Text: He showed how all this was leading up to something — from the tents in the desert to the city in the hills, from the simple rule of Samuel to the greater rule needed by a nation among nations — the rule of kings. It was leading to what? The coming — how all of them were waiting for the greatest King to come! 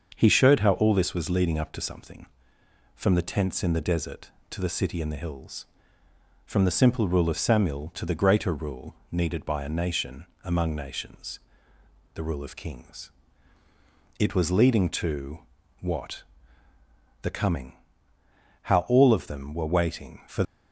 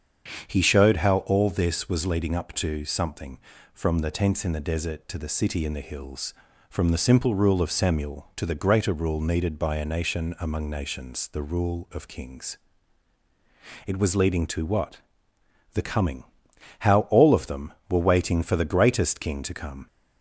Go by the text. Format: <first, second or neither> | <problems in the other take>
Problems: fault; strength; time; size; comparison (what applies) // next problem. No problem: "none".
second | starts louder than the rest; until 1.1 s; 6.5 dB; strong in the second // pauses between "rule" and "needed"; slight; at 8.9 s; 0.16 s long // pauses between "nation" and "among"; slight; at 10.2 s; 0.20 s long // pauses between "to" and "what"; at 15.3 s; 0.42 s long // stops before "the greatest King to come"; at 20.4 s